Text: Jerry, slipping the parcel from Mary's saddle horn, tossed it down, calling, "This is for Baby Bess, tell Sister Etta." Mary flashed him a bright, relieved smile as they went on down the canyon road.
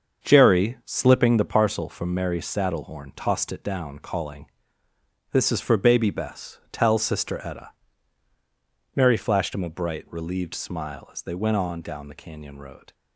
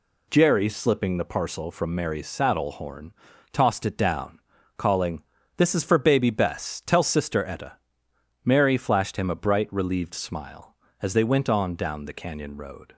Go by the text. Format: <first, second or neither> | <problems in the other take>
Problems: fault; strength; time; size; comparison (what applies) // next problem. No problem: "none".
second | starts louder than the rest; until 1.5 s; 6.5 dB